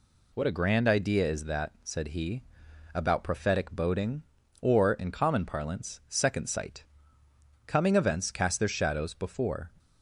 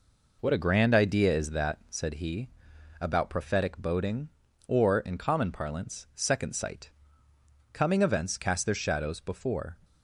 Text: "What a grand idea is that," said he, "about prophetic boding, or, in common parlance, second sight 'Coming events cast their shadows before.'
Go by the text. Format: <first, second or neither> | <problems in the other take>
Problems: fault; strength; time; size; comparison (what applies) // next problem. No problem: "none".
first | starts louder than the rest; noticeable; until 2.3 s; 4.5 dB // pauses between "sight" and "Coming"; noticeable; at 6.9 s; 0.82 s long; noticeable in the first